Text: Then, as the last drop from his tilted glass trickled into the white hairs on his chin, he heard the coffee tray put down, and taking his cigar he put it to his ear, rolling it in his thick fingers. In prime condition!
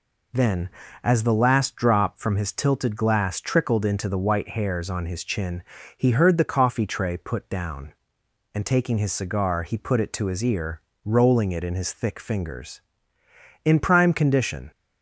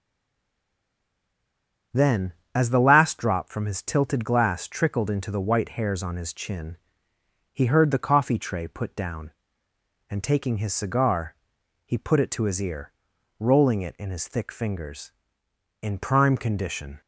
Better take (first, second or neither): first